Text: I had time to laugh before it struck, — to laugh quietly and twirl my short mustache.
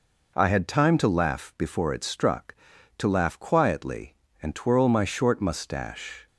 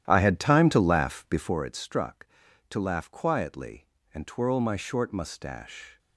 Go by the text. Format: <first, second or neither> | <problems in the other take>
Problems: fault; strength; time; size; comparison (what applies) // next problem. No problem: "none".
first | starts louder than the rest; strong; until 1.7 s; 11.5 dB